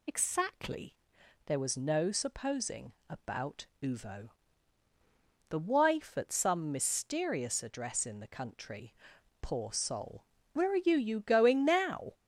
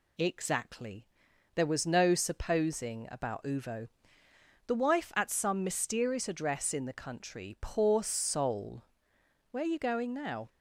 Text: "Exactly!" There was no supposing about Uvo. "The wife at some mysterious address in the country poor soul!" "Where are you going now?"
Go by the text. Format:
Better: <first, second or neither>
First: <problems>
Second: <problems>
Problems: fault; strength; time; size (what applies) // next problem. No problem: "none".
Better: second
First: pauses between "supposing" and "about"; slight; at 2.9 s; 0.18 s long // pauses between "country" and "poor"; noticeable; at 8.9 s; 0.48 s long // says "you" twice; at 10.9 s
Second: none